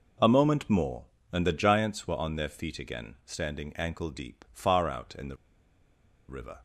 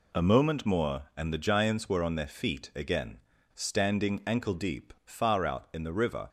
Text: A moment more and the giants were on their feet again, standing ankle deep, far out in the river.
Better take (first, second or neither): second